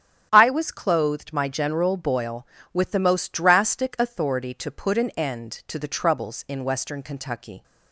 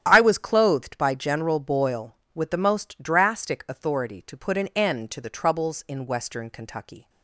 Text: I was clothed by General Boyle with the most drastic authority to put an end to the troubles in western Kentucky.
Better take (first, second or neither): second